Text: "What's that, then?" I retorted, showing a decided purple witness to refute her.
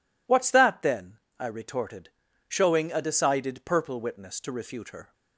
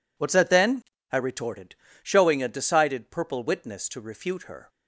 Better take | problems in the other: neither | none

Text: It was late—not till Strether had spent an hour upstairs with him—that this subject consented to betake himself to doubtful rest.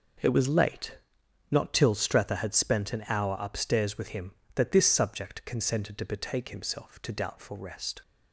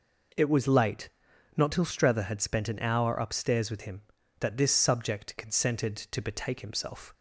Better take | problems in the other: first | stops before "to doubtful rest"; at 7.1 s

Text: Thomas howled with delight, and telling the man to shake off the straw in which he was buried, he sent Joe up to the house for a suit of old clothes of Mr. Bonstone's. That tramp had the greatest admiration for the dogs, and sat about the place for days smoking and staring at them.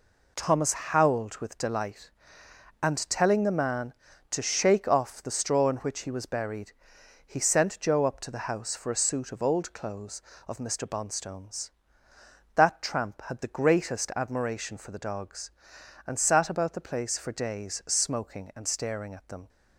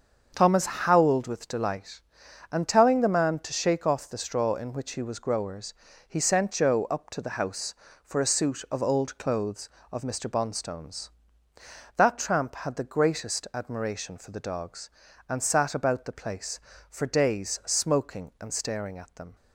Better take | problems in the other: first | starts louder than the rest; until 1.3 s; 6.5 dB // says "growers" for "buried"; at 5.1 s

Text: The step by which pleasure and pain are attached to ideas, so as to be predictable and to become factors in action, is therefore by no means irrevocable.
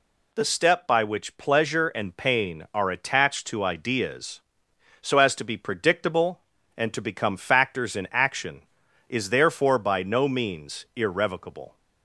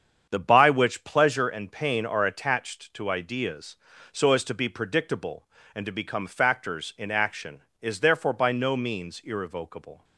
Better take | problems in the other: first | starts louder than the rest; strong; until 1.3 s; 7.5 dB // skips "step"; at 0.3 s

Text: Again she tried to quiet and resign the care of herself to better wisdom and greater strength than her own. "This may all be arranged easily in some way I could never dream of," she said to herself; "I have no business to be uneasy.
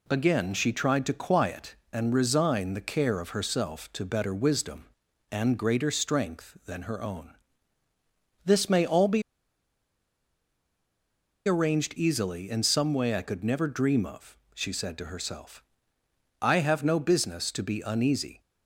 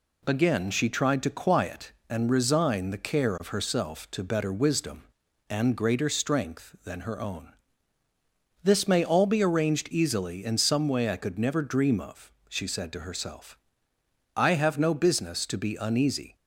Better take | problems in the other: second | pauses between "be" and "arranged"; strong; at 9.2 s; 2.2 s long

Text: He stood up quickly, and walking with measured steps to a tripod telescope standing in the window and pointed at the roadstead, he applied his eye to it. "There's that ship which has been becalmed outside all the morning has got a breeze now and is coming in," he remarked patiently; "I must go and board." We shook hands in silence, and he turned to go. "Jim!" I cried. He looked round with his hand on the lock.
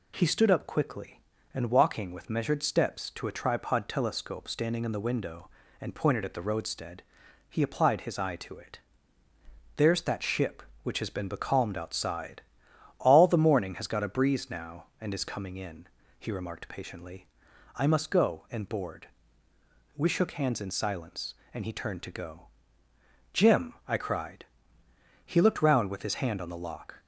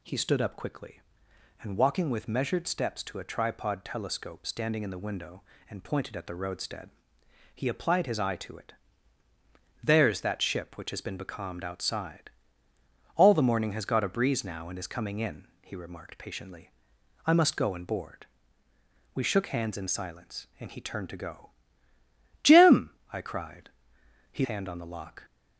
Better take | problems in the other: first | pauses between "outside" and "all"; noticeable; at 12.3 s; 0.84 s long; noticeable in the first // skips "looked round with his"; at 24.4 s

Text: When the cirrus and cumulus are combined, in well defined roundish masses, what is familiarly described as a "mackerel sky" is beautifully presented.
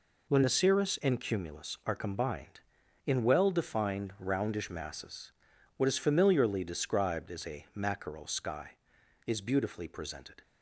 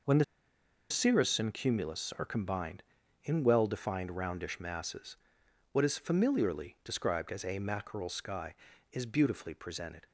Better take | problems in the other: first | pauses between "the" and "cirrus"; noticeable; at 0.2 s; 0.66 s long

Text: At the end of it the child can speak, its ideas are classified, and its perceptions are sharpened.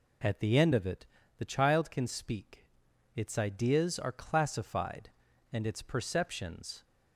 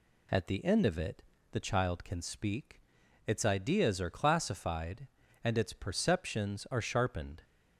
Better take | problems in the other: second | pauses between "it" and "the"; slight; at 1.0 s; 0.32 s long; slight in the second // stops before "are sharpened"; at 6.8 s

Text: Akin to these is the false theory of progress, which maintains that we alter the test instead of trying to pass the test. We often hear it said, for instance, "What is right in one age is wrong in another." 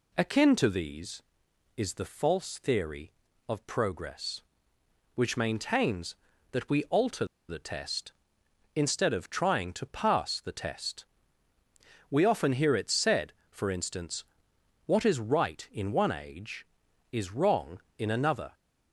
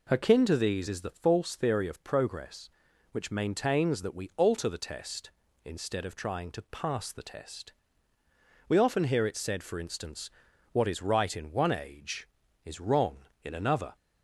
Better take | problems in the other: second | pauses between "alter" and "the"; slight; at 7.2 s; 0.24 s long

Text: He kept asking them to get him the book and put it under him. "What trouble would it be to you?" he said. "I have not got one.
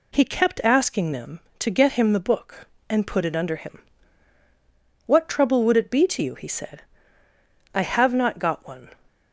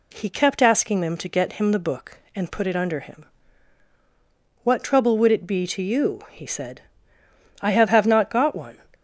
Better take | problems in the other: first | says "have" twice; at 7.8 s

